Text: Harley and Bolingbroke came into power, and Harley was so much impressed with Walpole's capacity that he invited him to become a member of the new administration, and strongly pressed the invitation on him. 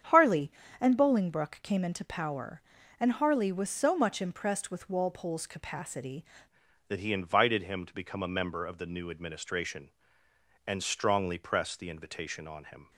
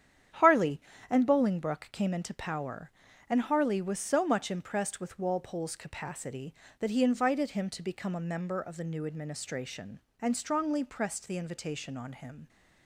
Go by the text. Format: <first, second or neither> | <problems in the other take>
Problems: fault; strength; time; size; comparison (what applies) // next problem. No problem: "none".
second | starts louder than the rest; strong; until 1.3 s; 8 dB; strong in the second // changes voice at "that"; from 6.8 s on; 6.1 s long